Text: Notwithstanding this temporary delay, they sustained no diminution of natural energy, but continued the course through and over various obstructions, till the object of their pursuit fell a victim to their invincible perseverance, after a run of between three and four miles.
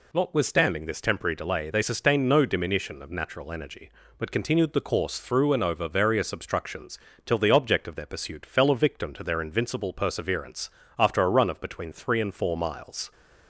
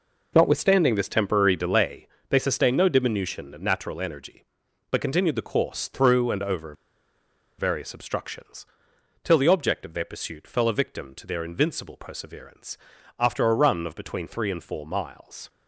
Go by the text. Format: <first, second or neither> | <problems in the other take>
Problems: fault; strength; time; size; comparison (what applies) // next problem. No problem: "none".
first | pauses between "over" and "various"; noticeable; at 6.7 s; 0.84 s long